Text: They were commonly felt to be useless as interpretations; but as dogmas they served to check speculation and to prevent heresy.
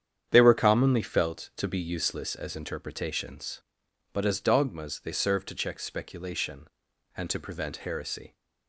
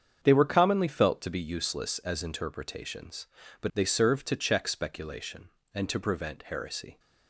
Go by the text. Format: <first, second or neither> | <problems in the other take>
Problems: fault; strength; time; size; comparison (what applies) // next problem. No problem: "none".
first | starts louder than the rest; strong; until 1.2 s; 7.5 dB; strong in the first // skips "as dogmas"; at 3.7 s